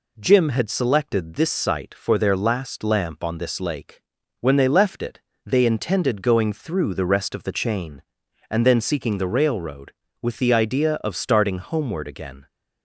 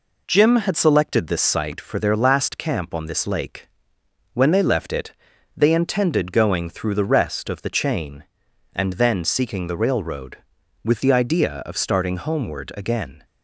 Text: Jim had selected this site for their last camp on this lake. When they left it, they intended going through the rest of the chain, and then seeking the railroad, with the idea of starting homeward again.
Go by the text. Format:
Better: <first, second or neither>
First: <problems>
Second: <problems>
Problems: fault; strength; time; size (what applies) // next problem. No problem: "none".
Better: second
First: says "lamp" for "camp"; at 2.8 s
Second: none